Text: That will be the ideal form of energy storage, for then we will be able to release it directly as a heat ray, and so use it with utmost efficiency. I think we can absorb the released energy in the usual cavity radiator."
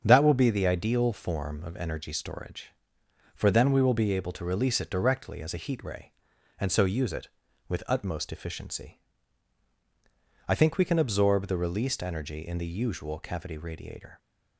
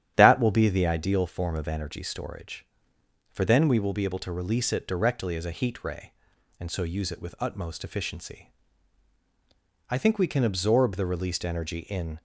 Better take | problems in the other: first | starts louder than the rest; strong; until 1.1 s; 10.5 dB; strong in the first // stops before "the usual cavity radiator"; at 12.1 s

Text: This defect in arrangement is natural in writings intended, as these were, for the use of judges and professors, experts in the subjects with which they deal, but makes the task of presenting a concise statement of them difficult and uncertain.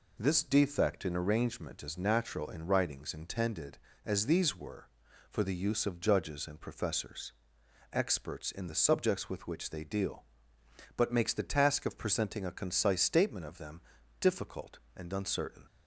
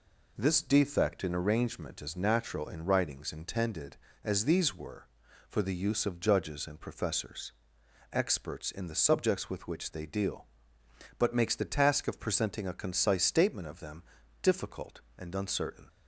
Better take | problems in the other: neither | pauses between "them" and "difficult"; the same in both

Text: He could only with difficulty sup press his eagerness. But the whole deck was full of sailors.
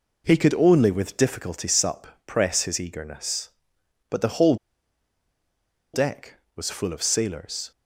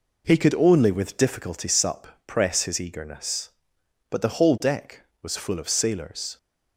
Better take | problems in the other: second | pauses between "sup" and "press"; slight; at 2.0 s; 0.18 s long; slight in the second // pauses between "whole" and "deck"; strong; at 4.5 s; 1.3 s long

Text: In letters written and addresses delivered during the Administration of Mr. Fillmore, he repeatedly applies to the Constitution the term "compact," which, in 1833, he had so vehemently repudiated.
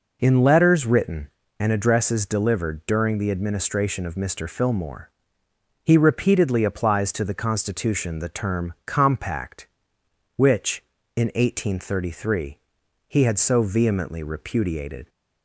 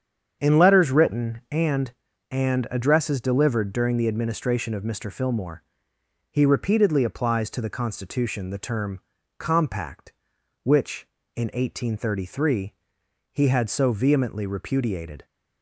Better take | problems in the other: first | starts louder than the rest; strong; until 1.4 s; 7.5 dB // says "and" twice; at 2.3 s // pauses between "term" and "compact"; slight; at 9.0 s; 0.36 s long

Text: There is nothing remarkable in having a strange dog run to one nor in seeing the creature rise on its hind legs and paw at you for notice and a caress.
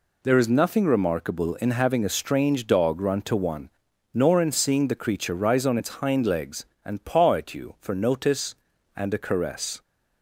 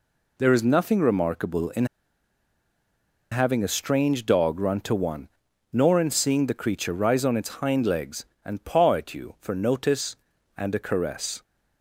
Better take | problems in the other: first | pauses between "in" and "having"; strong; at 1.8 s; 1.4 s long // pauses between "one" and "nor"; at 5.2 s; 0.42 s long; also in the first

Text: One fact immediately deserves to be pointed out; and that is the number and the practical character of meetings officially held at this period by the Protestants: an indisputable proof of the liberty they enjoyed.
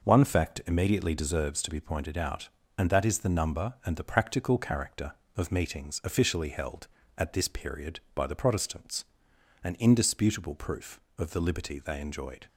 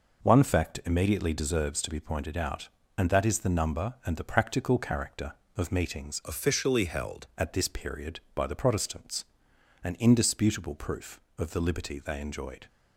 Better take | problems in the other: first | changes voice from "officially" to "held"; from 6.2 to 7.2 s; 1.0 s long

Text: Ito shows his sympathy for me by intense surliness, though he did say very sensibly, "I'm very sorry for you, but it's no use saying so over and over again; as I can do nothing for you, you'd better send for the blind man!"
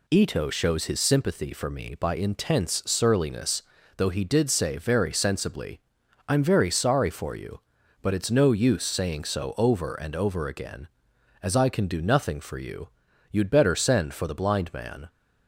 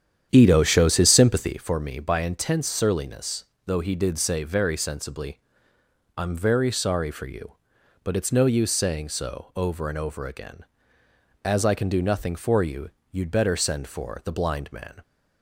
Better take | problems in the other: first | starts louder than the rest; strong; until 1.7 s; 9.5 dB

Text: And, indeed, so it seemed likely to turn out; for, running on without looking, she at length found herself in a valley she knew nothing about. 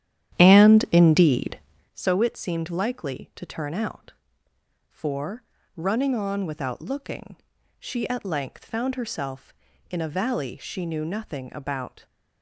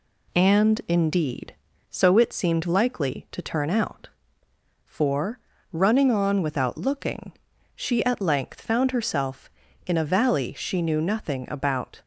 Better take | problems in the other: second | starts louder than the rest; strong; until 1.9 s; 11 dB

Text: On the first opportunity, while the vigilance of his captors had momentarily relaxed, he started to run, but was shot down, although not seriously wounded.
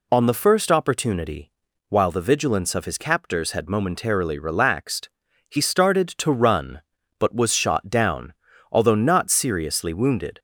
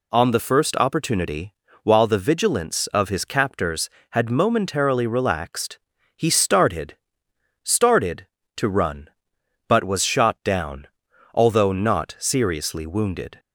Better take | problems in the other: first | says "started" twice; at 7.6 s

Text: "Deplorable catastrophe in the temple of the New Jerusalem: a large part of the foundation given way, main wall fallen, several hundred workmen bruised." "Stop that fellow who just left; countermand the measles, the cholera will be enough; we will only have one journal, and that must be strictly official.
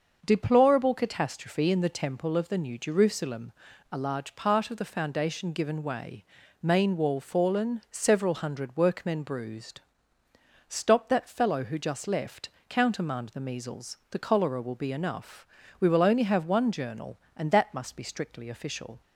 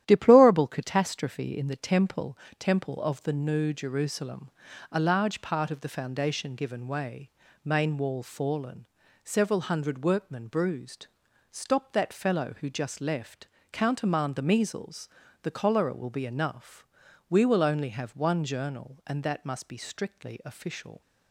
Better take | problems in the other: first | starts louder than the rest; strong; until 1.0 s; 11.5 dB; also in the first // says "temple" twice; at 2.5 s

